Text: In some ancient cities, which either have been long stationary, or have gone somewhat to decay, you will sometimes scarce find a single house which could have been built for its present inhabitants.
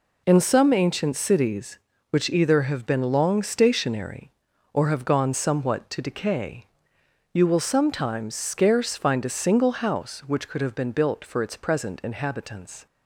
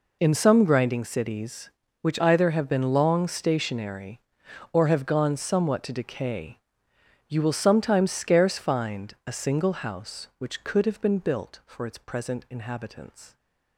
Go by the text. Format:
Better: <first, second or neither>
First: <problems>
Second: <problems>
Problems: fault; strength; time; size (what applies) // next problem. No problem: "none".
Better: first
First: none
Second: says "grinding" for "ancient"; at 0.6 s